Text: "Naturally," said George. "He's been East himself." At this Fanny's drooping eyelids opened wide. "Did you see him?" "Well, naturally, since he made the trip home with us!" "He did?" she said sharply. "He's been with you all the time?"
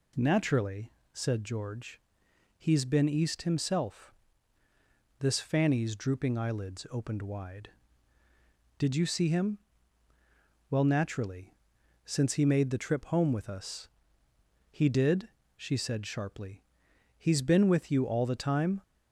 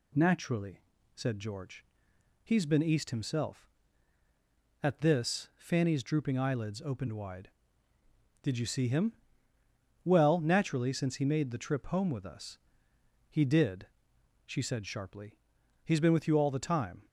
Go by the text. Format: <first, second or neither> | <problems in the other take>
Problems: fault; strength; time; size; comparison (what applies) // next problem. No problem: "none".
second | skips "At"; at 4.6 s